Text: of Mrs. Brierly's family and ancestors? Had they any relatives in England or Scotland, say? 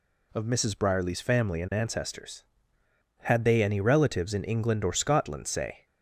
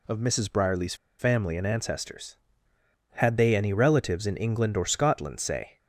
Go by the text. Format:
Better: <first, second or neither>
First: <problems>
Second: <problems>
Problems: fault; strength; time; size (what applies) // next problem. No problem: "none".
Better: first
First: none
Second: pauses between "Brierly's" and "family"; slight; at 0.9 s; 0.24 s long